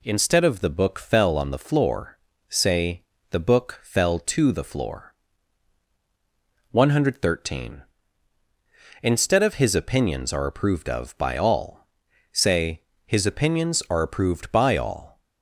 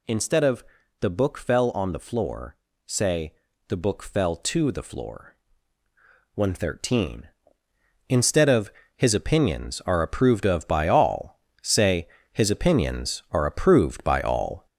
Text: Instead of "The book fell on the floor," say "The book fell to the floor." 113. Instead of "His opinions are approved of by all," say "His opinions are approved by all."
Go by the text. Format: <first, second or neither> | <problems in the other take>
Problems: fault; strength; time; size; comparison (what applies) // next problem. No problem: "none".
first | gets louder; noticeable; throughout; 4.5 dB // pauses between "of" and "The"; slight; at 0.6 s; 0.36 s long // pauses between "say" and "The"; slight; at 3.3 s; 0.36 s long; slight in the first // pauses between "of" and "His"; slight; at 8.7 s; 0.26 s long // pauses between "say" and "His"; slight; at 12.0 s; 0.28 s long; slight in the first